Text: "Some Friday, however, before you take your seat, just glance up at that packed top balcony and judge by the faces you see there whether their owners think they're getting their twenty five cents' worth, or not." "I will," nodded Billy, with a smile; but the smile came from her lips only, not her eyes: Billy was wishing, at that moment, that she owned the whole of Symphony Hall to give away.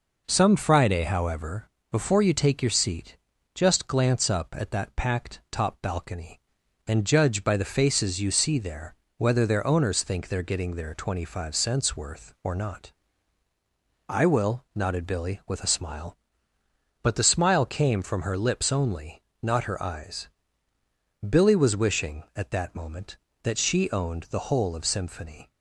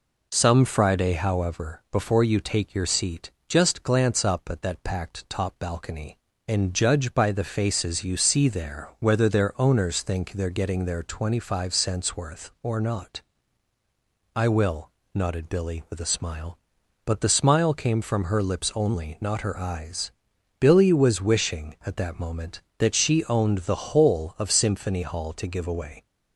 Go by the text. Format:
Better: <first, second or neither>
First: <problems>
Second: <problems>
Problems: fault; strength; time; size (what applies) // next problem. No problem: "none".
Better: second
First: pauses between "there" and "whether"; slight; at 8.9 s; 0.22 s long // stops before "Hall to give away"; at 25.5 s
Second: none